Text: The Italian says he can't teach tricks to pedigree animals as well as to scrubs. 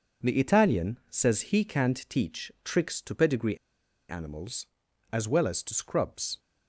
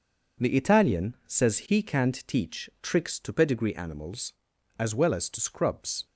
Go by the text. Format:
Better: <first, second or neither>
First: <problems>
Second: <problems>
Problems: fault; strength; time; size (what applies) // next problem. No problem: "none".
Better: second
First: pauses between "pedigree" and "animals"; noticeable; at 3.5 s; 0.51 s long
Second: none